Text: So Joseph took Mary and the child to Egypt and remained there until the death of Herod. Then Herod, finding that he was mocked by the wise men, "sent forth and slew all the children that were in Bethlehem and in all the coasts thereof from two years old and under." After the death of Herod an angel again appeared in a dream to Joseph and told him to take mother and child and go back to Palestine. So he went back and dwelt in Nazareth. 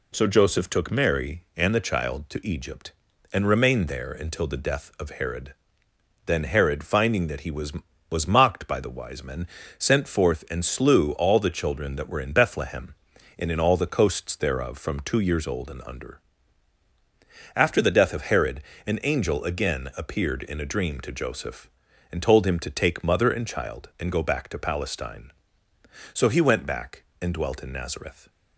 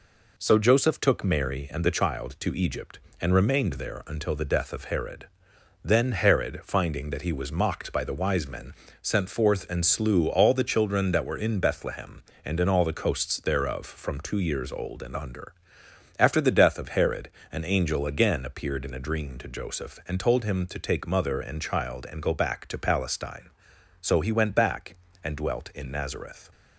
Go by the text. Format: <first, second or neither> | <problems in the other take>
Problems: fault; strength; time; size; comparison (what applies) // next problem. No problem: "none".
second | says "was" twice; at 8.1 s // pauses between "Herod" and "an"; slight; at 18.6 s; 0.24 s long; slight in the second